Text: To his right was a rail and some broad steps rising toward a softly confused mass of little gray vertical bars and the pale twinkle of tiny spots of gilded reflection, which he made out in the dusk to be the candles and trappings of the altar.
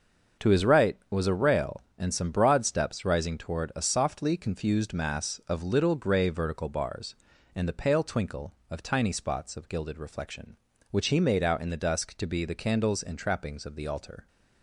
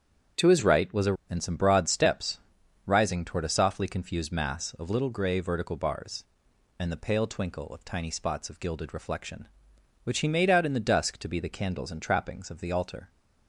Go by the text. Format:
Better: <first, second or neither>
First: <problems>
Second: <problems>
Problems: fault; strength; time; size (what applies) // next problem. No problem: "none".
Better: first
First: starts louder than the rest; until 1.5 s; 6.5 dB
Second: starts louder than the rest; strong; until 1.5 s; 8 dB // skips "rail"; at 1.2 s // pauses between "steps" and "rising"; noticeable; at 2.4 s; 0.46 s long